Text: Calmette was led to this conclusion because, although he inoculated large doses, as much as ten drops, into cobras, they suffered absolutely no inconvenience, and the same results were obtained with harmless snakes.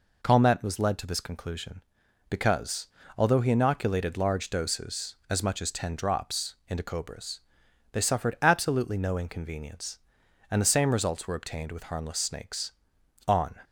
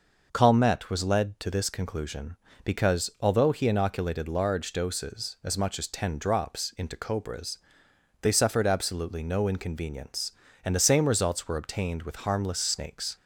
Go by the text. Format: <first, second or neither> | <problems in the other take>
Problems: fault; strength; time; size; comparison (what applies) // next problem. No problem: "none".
second | goes on to say "On"; slight; from 13.2 s on; 0.30 s long